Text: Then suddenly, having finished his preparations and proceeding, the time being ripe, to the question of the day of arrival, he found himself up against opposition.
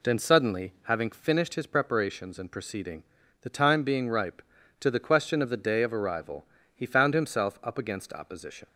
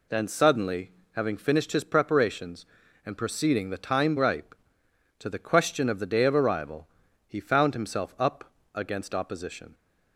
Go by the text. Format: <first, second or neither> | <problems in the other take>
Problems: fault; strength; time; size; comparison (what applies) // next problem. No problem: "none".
first | skips "being"; at 4.1 s // pauses between "up" and "against"; slight; at 8.5 s; 0.22 s long